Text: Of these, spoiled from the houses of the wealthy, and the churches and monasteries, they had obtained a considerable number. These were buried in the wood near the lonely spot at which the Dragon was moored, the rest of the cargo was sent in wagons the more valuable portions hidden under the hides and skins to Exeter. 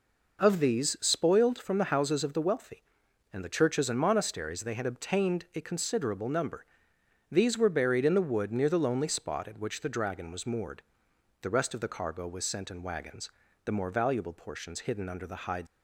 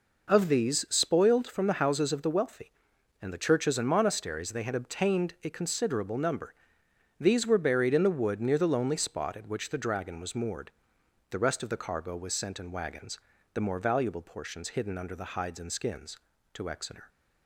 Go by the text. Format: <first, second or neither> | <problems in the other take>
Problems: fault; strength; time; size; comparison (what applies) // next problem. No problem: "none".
second | pauses between "wagons" and "the"; slight; at 13.2 s; 0.36 s long; slight in the second // stops before "and skins to Exeter"; at 15.6 s